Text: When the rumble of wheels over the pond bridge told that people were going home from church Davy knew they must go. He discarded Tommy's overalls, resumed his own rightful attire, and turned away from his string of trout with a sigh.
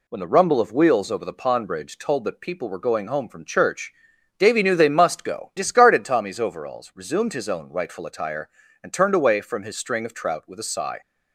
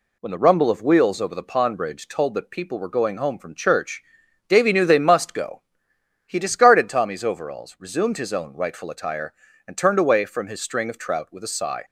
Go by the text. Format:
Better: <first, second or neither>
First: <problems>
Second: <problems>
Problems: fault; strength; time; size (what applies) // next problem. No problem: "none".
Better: second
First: pauses between "church" and "Davy"; at 3.9 s; 0.44 s long // skips "He"; at 5.5 s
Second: pauses between "church" and "Davy"; at 4.0 s; 0.44 s long